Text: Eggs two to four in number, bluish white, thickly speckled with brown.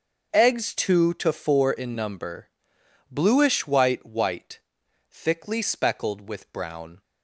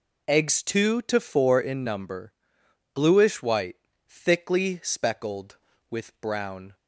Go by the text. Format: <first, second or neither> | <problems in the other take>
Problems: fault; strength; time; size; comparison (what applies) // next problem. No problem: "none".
second | starts louder than the rest; until 1.3 s; 6.5 dB // says "white" twice; at 4.0 s